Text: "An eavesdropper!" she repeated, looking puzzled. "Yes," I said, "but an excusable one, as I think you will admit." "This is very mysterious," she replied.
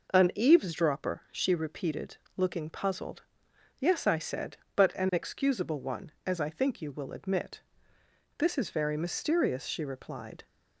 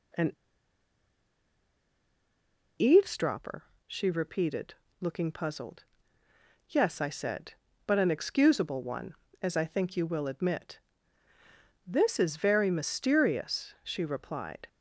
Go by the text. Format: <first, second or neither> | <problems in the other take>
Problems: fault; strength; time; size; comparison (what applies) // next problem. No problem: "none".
first | pauses between "An" and "eavesdropper"; strong; at 0.3 s; 2.4 s long